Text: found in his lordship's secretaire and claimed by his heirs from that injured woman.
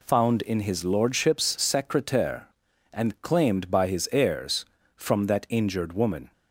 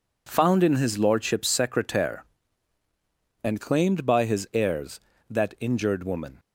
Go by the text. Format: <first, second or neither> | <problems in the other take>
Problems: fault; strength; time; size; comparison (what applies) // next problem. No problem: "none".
first | skips "from"; at 5.1 s